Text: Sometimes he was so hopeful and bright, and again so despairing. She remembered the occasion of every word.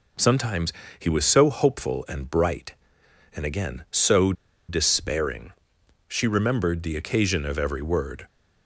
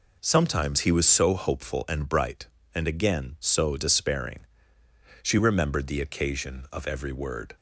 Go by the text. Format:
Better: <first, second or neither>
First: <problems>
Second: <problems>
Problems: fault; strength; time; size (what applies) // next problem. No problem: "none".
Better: second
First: pauses between "Sometimes" and "he"; slight; at 0.7 s; 0.26 s long // pauses between "so" and "despairing"; at 4.3 s; 0.36 s long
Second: none